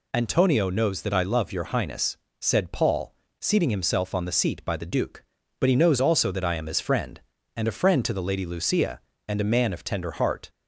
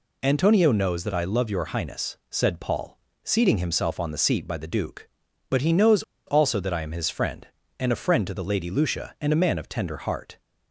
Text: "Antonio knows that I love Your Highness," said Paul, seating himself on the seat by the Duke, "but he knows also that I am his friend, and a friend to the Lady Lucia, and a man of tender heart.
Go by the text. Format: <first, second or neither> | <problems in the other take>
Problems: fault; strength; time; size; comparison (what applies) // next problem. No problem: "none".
first | pauses between "knows" and "also"; slight; at 6.0 s; 0.25 s long